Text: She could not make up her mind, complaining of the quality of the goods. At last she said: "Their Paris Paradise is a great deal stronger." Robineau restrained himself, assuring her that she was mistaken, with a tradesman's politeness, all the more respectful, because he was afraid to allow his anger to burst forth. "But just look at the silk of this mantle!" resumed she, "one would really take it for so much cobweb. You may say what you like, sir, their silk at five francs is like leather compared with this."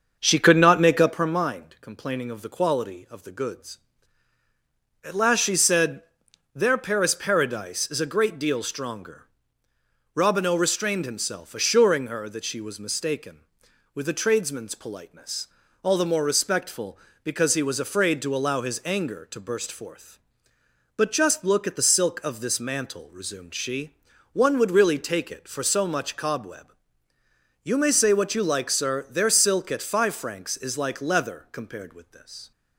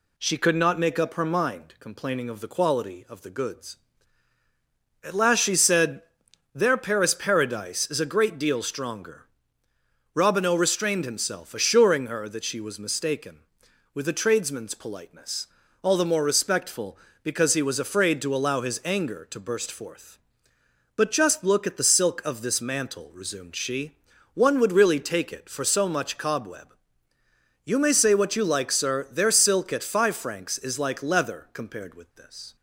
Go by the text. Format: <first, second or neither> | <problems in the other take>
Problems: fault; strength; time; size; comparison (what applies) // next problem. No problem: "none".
second | starts louder than the rest; until 1.4 s; 6.5 dB